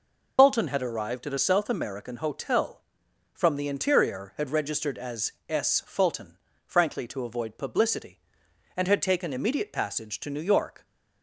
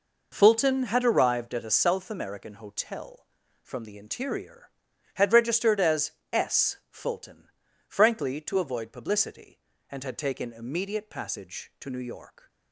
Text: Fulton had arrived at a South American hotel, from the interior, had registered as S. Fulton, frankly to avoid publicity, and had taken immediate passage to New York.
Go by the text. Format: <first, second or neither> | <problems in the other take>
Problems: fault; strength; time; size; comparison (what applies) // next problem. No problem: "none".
second | loses the start of "Fulton"; at 0.3 s; 130 ms // pauses between "as" and "S"; slight; at 5.3 s; 0.16 s long; slight in the second